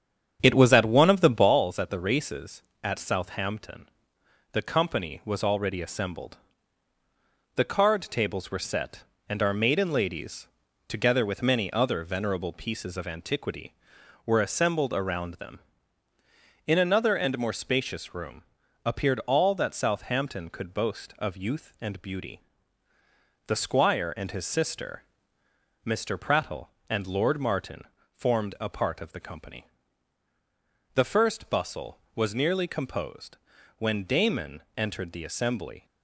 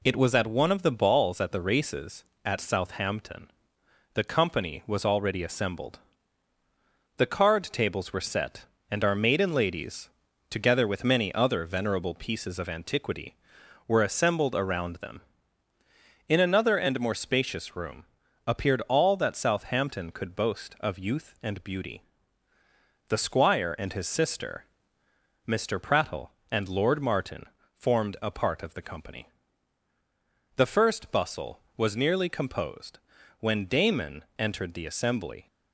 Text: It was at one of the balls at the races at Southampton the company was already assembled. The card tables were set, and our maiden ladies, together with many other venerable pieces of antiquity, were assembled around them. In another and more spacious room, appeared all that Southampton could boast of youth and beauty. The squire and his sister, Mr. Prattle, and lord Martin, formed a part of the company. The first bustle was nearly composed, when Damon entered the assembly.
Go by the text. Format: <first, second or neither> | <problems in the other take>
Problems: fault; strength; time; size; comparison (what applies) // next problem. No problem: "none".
second | starts louder than the rest; strong; until 1.6 s; 8 dB // pauses between "Southampton" and "the"; noticeable; at 3.8 s; 0.66 s long; noticeable in the second // pauses between "Damon" and "entered"; slight; at 34.6 s; 0.16 s long; slight in the second